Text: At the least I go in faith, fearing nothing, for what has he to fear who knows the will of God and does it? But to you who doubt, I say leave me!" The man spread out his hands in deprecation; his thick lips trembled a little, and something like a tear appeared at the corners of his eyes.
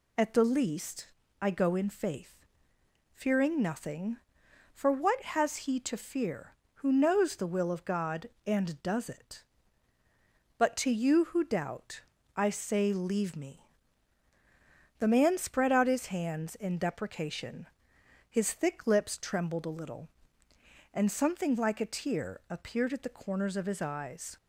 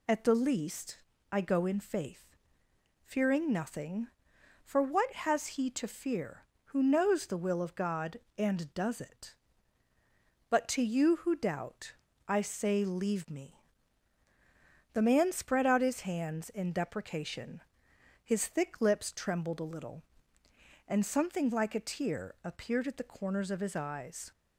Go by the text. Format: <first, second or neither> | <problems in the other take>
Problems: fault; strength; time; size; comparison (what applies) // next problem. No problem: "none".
neither | pauses between "least" and "I"; slight; the same in both